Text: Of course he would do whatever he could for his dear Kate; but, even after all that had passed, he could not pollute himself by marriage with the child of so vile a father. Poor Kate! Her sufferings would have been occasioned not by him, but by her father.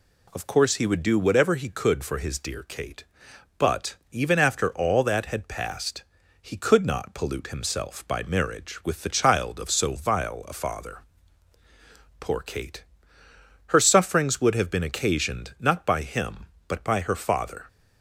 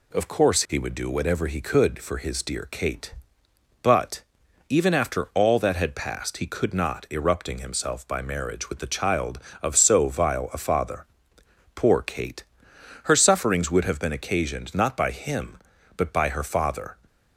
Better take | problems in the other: first | says "erupting" for "pollute"; at 7.0 s

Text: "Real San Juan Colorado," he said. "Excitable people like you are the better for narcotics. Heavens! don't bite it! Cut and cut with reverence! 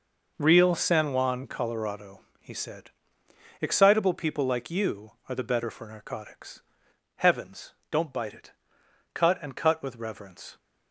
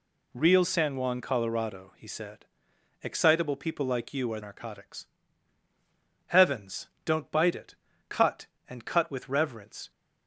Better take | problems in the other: first | skips "the better for"; at 4.3 s

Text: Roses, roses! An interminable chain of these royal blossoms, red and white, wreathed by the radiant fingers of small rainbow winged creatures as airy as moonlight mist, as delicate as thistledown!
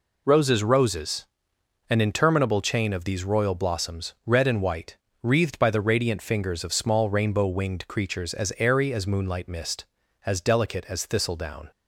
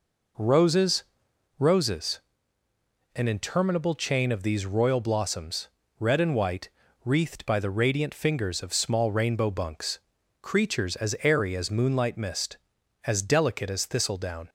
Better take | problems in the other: first | says "bunks" for "winged"; at 9.4 s

